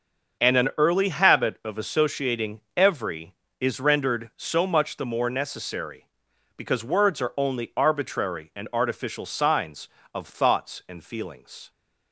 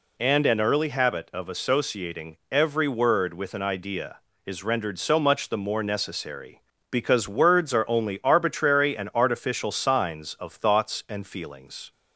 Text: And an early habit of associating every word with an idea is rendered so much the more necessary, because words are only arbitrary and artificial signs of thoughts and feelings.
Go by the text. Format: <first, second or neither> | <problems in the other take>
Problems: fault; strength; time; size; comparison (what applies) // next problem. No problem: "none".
second | starts louder than the rest; until 1.4 s; 6.5 dB // pauses between "associating" and "every"; slight; at 2.6 s; 0.16 s long // skips "word with an idea"; at 3.4 s